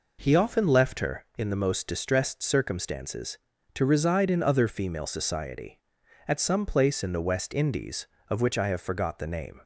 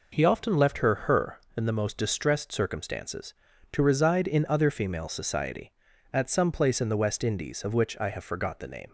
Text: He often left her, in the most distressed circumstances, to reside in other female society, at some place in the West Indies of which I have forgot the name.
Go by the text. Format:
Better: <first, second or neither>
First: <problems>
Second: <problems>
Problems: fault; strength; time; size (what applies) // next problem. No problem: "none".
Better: first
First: none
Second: says "her" twice; at 1.0 s